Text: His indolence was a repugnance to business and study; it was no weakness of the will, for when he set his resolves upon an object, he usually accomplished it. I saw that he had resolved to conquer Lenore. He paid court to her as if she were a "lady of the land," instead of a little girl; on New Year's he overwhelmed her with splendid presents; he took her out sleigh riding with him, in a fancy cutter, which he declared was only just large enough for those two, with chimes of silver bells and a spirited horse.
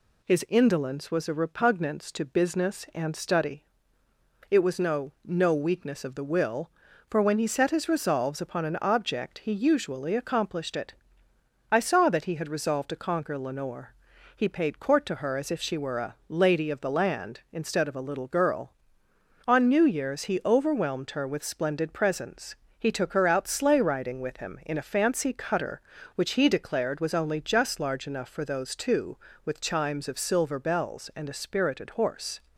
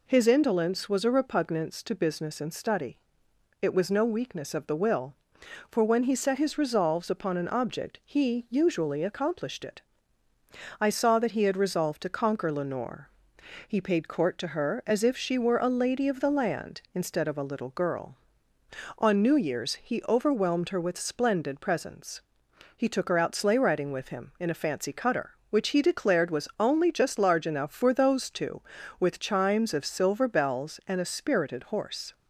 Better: second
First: says "no" twice; at 5.2 s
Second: none

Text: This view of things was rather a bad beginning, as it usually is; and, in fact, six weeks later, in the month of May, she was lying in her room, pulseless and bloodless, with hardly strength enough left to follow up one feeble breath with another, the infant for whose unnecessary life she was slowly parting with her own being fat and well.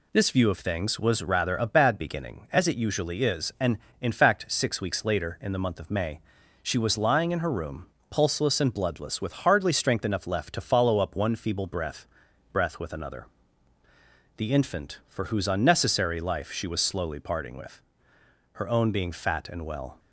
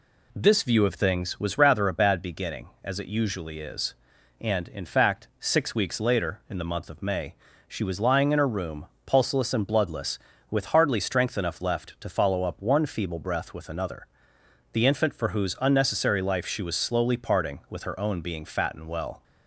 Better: second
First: says "breath" twice; at 12.5 s // pauses between "with" and "her"; noticeable; at 17.7 s; 0.74 s long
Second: none

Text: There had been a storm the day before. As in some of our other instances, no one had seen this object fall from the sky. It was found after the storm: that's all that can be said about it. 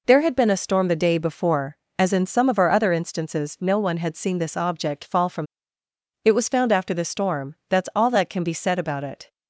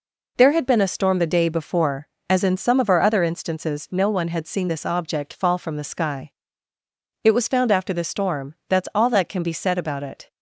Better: second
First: skips "the sky"; at 5.8 s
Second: none

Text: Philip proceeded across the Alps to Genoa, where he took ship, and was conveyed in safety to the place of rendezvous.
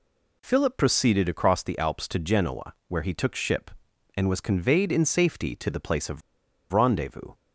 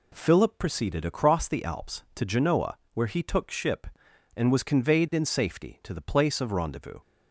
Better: second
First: pauses between "of" and "rendezvous"; noticeable; at 6.2 s; 0.51 s long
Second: none

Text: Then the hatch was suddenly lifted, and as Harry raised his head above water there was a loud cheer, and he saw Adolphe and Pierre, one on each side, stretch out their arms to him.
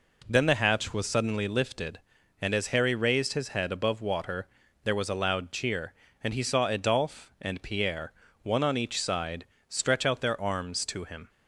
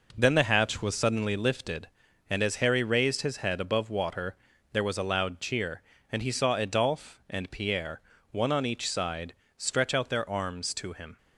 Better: first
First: pauses between "water" and "there"; at 4.4 s; 0.38 s long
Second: gets quieter; strong; throughout; 7.5 dB // pauses between "water" and "there"; at 4.3 s; 0.38 s long

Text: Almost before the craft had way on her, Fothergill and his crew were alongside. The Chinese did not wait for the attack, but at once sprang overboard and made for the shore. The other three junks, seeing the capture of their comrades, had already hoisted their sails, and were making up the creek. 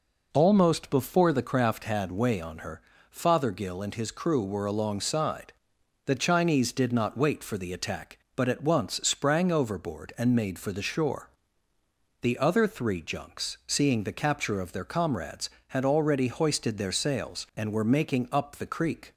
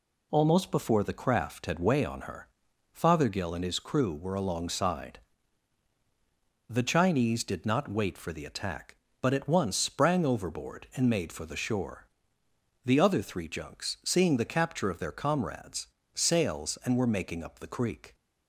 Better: first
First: none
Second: skips "had already hoisted their"; at 16.0 s

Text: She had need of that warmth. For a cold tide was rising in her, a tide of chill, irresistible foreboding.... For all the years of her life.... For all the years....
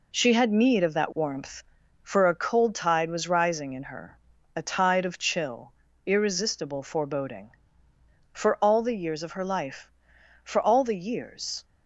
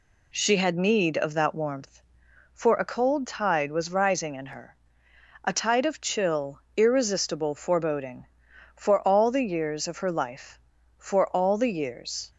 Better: neither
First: none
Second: none

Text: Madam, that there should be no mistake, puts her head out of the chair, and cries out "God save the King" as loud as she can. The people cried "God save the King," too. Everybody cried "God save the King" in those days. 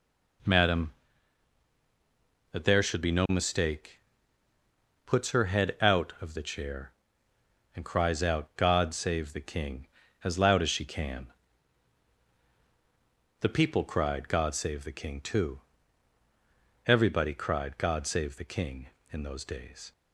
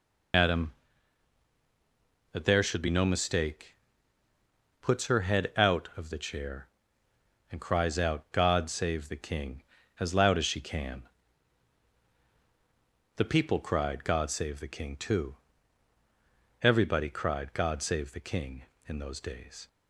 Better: first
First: none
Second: loses the start of "Madam"; at 0.3 s; 120 ms

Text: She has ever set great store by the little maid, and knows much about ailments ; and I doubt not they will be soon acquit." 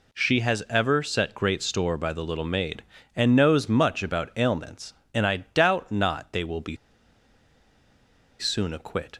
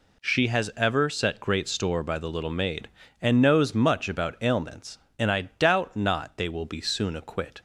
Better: second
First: pauses between "be" and "soon"; strong; at 6.7 s; 1.6 s long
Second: none

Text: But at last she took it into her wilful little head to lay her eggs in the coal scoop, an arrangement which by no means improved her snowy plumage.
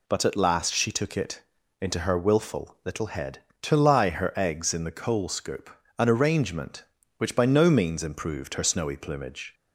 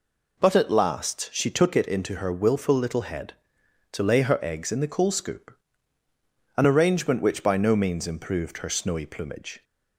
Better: second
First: pauses between "it" and "into"; at 1.4 s; 0.40 s long // says "lie" for "lay"; at 3.7 s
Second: none

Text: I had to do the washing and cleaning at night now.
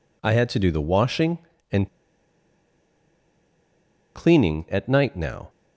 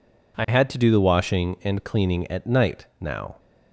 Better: second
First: pauses between "and" and "cleaning"; strong; at 1.8 s; 2.2 s long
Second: none

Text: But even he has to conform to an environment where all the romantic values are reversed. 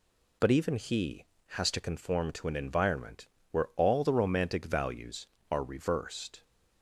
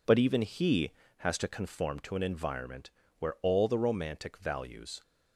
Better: first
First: pauses between "environment" and "where"; slight; at 3.2 s; 0.24 s long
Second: pauses between "environment" and "where"; slight; at 2.8 s; 0.28 s long // stops before "are reversed"; at 5.0 s

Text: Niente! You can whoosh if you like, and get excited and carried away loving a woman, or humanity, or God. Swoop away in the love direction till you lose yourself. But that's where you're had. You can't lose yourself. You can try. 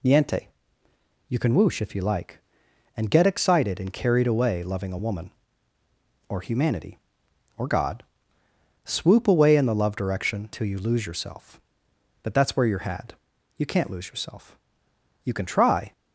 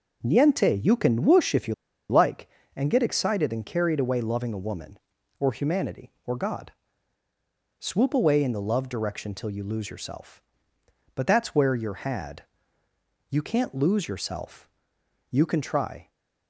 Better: first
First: none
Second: pauses between "you" and "like"; slight; at 1.7 s; 0.36 s long

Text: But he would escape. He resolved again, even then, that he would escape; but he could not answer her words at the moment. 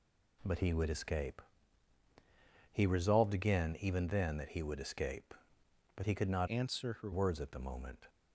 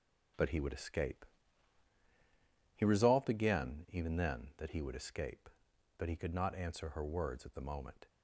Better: second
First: changes voice from "answer" to "her"; from 6.4 to 7.1 s; 0.7 s long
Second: none

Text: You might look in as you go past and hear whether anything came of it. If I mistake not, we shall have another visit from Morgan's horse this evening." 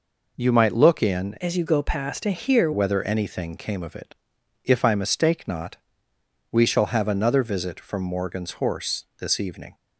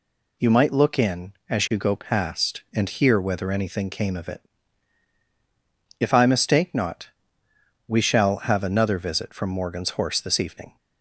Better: second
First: changes voice from "as" to "hear"; from 1.3 to 2.7 s; 1.4 s long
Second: none

